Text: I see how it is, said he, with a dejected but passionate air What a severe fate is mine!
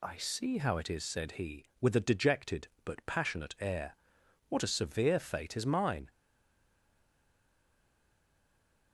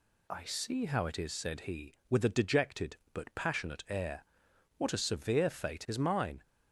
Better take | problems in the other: second | pauses between "air" and "What"; noticeable; at 3.9 s; 0.54 s long; noticeable in the second // stays silent after the last word; strong; from 6.1 s on; 2.8 s long

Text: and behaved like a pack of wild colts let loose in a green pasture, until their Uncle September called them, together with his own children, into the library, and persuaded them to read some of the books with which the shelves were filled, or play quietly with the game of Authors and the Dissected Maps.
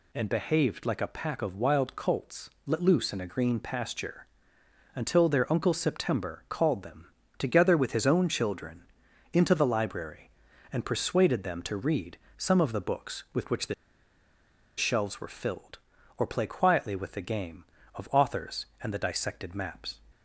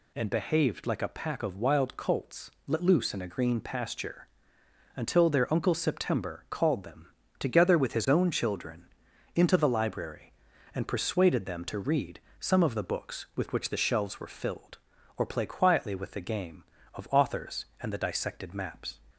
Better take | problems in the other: second | pauses between "colts" and "let"; slight; at 2.4 s; 0.16 s long; slight in the second // pauses between "read" and "some"; slight; at 12.1 s; 0.18 s long; slight in the second // pauses between "the" and "shelves"; at 13.7 s; 1.0 s long

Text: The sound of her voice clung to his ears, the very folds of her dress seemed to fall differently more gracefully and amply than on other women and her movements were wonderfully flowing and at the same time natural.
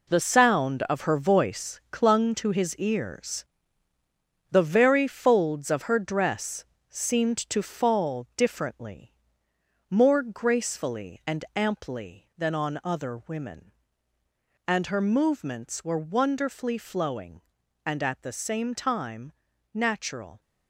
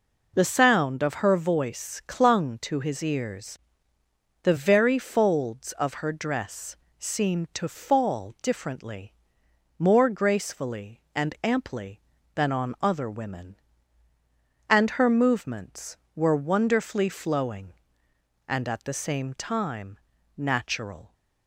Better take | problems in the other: second | gets quieter; strong; throughout; 9.5 dB // pauses between "dress" and "seemed"; slight; at 6.6 s; 0.24 s long; slight in the second // pauses between "differently" and "more"; noticeable; at 9.1 s; 0.78 s long; noticeable in the second // pauses between "time" and "natural"; at 19.3 s; 0.42 s long; also in the second

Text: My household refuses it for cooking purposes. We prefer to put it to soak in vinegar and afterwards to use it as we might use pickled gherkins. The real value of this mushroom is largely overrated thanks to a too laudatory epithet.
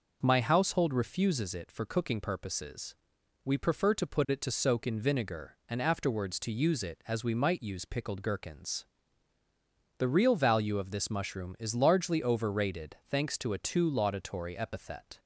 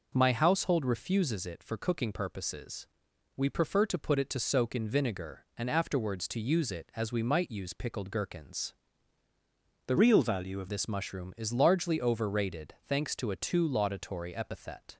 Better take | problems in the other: first | changes voice from "real" to "of"; from 9.9 to 10.6 s; 0.7 s long

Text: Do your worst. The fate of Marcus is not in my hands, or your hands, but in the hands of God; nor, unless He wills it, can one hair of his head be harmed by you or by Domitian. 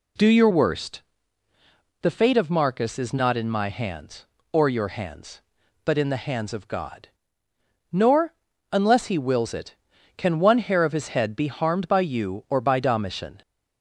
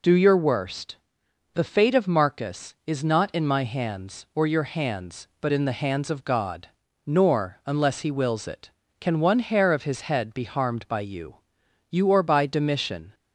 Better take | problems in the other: first | says "you" twice; at 11.8 s

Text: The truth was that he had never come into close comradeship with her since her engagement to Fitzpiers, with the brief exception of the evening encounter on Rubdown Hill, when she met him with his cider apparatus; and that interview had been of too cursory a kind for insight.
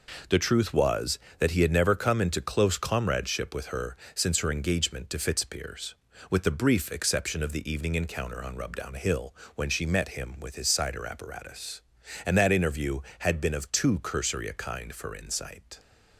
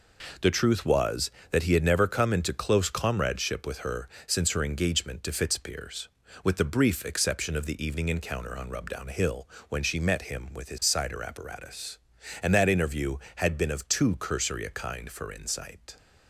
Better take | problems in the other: neither | pauses between "her" and "since"; slight; the same in both

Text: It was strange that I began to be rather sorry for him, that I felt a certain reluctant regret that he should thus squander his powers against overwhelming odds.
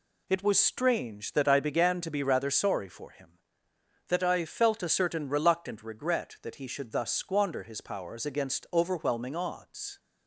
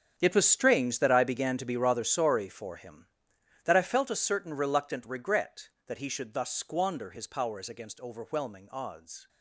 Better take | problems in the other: first | gets quieter; strong; throughout; 15 dB

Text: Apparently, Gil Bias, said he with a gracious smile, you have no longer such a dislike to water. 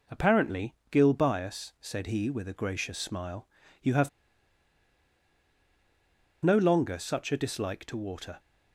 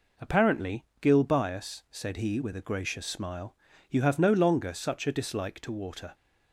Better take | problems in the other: second | pauses between "have" and "no"; strong; at 4.0 s; 2.3 s long

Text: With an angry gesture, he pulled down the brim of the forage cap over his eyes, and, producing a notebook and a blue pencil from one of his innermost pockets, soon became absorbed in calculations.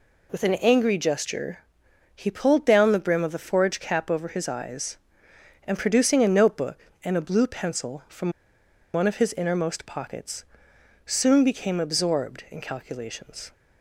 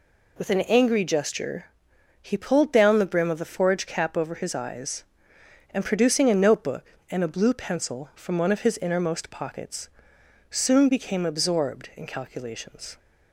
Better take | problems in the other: second | pauses between "from" and "one"; noticeable; at 8.3 s; 0.63 s long

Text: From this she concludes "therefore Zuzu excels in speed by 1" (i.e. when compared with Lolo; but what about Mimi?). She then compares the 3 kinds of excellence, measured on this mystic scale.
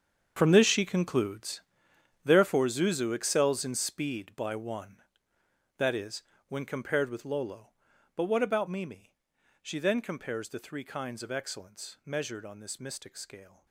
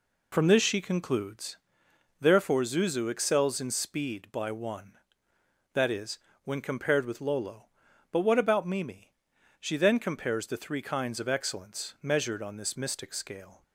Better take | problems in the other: second | gets quieter; strong; throughout; 15.5 dB // pauses between "concludes" and "therefore"; noticeable; at 1.6 s; 0.62 s long; noticeable in the second

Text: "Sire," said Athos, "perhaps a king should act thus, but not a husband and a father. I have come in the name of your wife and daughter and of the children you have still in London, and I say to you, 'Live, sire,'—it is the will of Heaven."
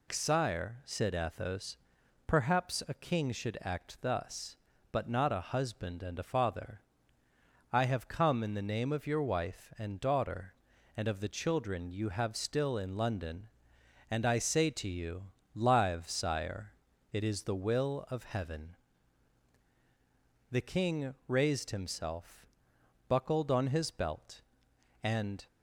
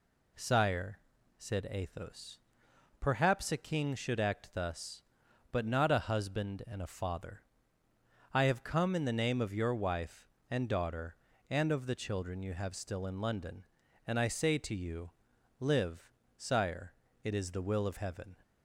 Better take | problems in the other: second | goes on to say "The king raised himself buckled on his belt and"; strong; from 20.5 s on; 4.9 s long

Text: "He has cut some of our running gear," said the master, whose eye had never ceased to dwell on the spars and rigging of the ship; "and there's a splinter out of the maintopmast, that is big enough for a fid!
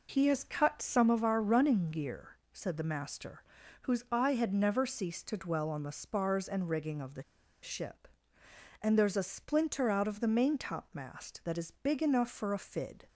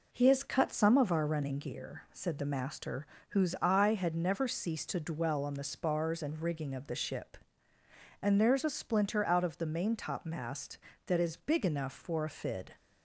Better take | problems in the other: second | pauses between "the" and "ship"; at 7.2 s; 0.40 s long

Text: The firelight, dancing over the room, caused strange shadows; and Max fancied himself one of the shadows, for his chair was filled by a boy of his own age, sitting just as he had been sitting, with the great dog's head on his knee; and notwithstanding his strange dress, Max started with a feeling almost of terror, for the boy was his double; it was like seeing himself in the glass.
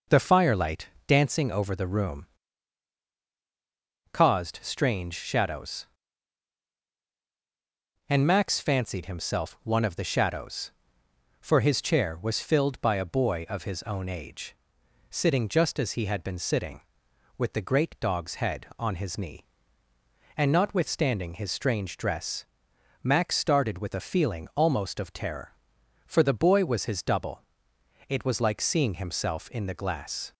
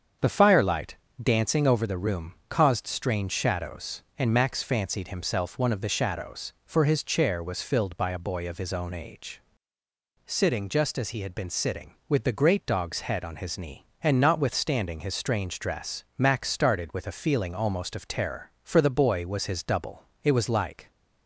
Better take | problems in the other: first | starts louder than the rest; strong; until 1.4 s; 7.5 dB // stops before "seeing himself in the glass"; at 20.9 s

